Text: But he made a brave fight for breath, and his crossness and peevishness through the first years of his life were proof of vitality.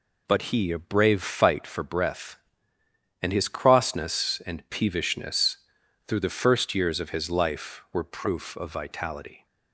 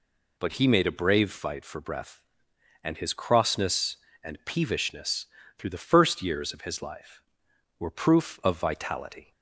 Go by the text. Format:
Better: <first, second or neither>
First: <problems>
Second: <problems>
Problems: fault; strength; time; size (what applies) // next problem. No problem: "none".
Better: second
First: skips "made"; at 0.7 s // pauses between "peevishness" and "through"; noticeable; at 5.5 s; 0.50 s long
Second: pauses between "peevishness" and "through"; slight; at 5.2 s; 0.32 s long